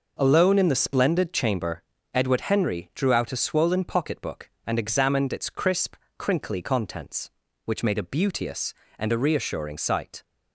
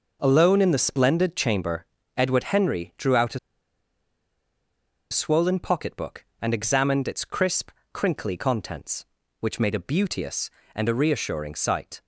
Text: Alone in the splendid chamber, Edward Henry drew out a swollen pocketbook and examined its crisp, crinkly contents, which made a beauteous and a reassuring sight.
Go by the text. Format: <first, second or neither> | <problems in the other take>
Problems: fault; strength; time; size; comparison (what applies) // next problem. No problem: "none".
first | pauses between "a" and "swollen"; strong; at 3.3 s; 1.7 s long